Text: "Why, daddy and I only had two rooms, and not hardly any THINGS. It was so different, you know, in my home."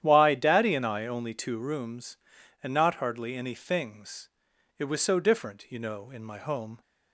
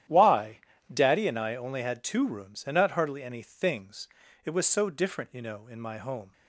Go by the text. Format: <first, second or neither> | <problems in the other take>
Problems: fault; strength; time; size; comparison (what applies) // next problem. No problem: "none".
second | starts louder than the rest; strong; until 1.0 s; 10.5 dB; strong in the second // skips "had"; at 1.3 s